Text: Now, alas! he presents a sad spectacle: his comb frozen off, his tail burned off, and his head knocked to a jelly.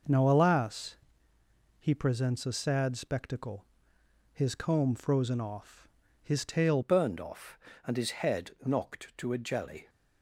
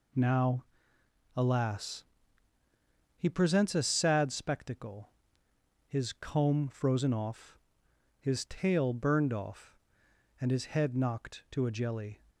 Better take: second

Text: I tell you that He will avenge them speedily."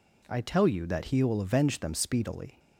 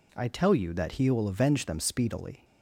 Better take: neither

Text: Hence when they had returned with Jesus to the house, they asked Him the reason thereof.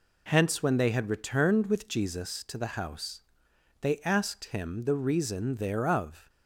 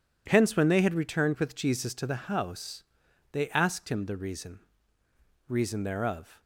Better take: first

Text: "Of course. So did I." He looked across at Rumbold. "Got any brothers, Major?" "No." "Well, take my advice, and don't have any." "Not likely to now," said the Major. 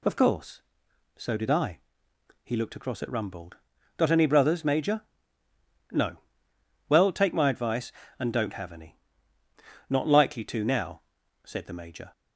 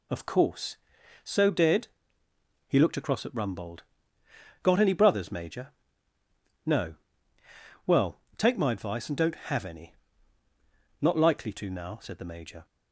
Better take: first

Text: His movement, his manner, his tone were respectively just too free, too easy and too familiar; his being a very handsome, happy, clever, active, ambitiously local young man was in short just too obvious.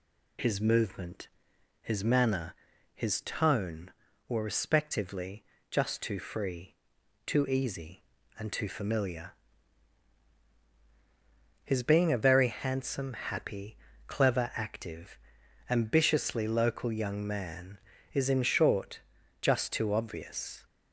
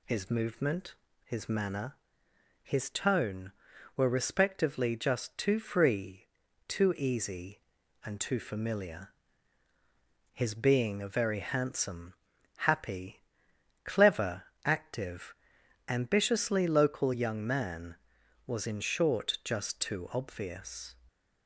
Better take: second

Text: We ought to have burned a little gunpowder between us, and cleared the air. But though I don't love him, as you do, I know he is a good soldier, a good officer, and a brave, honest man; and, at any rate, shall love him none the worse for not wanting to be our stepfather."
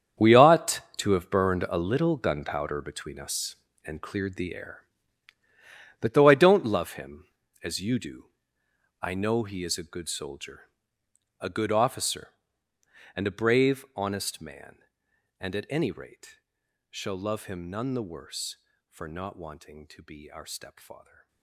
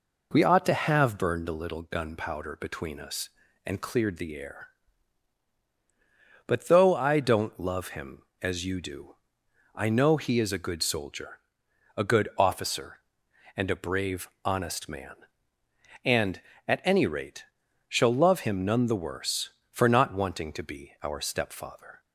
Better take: second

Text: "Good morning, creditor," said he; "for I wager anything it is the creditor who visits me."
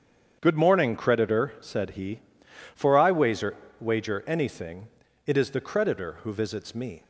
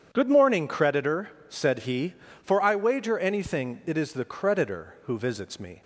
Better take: second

